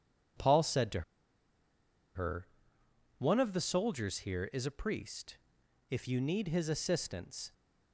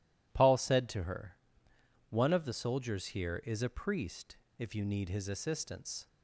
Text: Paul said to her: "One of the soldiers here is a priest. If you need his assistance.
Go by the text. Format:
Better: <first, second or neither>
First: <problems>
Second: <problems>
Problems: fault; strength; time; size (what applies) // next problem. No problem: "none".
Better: second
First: pauses between "to" and "her"; at 1.0 s; 1.1 s long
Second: none